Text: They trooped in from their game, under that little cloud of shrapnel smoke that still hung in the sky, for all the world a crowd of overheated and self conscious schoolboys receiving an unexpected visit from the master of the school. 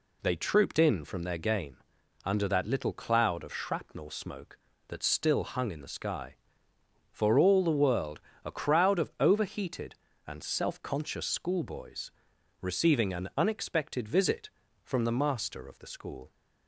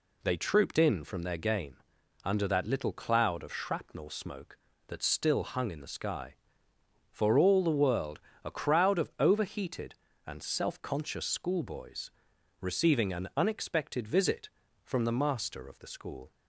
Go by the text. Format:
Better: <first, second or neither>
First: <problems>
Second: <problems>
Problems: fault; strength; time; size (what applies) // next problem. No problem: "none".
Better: neither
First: pauses between "world" and "a"; slight; at 8.1 s; 0.24 s long // pauses between "schoolboys" and "receiving"; noticeable; at 12.1 s; 0.48 s long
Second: pauses between "world" and "a"; slight; at 8.1 s; 0.24 s long // pauses between "schoolboys" and "receiving"; noticeable; at 12.1 s; 0.48 s long